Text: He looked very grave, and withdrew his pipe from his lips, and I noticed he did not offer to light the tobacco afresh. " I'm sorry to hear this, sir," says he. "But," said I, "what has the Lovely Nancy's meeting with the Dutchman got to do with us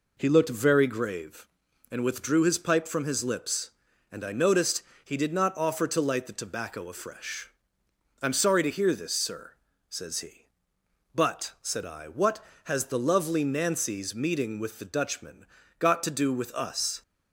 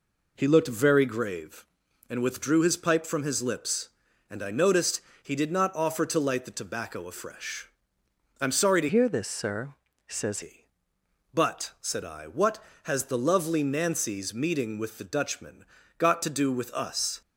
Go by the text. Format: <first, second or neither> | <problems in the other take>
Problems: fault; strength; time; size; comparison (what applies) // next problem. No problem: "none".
first | pauses between "noticed" and "he"; slight; at 5.0 s; 0.22 s long; slight in the first // changes voice from "hear" to "says"; from 8.8 to 10.4 s; 1.6 s long // pauses between "Dutchman" and "got"; slight; at 15.6 s; 0.36 s long; slight in the first